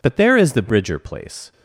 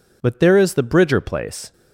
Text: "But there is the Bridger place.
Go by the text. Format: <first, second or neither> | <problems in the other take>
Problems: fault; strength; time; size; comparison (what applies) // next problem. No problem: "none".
neither | none